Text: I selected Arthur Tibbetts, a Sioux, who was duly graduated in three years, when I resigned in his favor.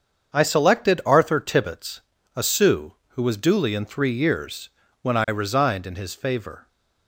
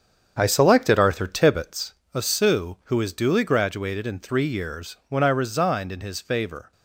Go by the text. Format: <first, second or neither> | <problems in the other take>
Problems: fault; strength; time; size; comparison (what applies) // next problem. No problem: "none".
second | starts louder than the rest; until 1.4 s; 7 dB; strong in the second // skips "graduated"; at 3.7 s